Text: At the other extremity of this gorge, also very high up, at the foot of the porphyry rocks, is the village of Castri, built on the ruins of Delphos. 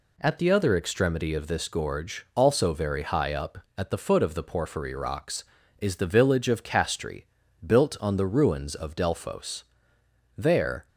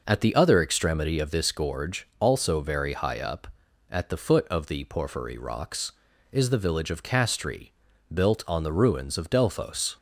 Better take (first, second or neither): second